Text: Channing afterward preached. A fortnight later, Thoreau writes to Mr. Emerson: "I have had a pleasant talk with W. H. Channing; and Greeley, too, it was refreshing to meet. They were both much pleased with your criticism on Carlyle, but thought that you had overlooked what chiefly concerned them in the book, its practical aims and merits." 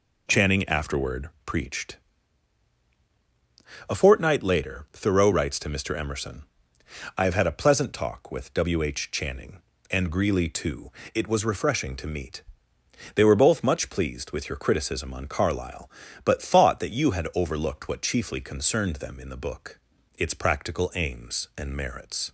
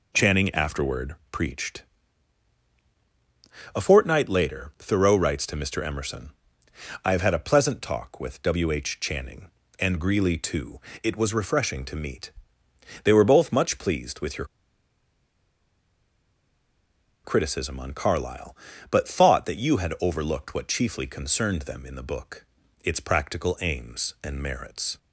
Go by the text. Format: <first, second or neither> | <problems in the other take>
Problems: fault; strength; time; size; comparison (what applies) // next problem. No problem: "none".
first | pauses between "afterward" and "preached"; slight; at 1.1 s; 0.16 s long; slight in the first // pauses between "your" and "criticism"; strong; at 14.4 s; 2.7 s long